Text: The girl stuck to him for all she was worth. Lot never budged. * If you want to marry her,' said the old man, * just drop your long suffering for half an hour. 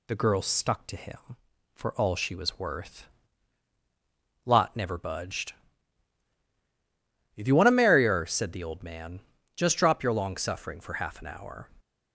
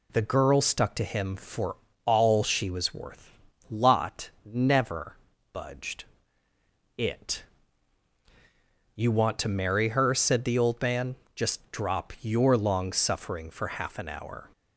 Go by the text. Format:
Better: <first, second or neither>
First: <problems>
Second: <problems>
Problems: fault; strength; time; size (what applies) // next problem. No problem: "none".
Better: first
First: none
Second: pauses between "for" and "all"; slight; at 1.7 s; 0.28 s long // pauses between "never" and "budged"; at 5.1 s; 0.38 s long // says "It" for "If"; at 6.9 s